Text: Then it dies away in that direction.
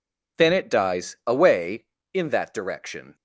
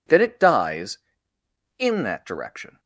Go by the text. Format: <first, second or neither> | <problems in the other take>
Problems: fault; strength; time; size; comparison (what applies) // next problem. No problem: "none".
first | skips "away"; at 1.3 s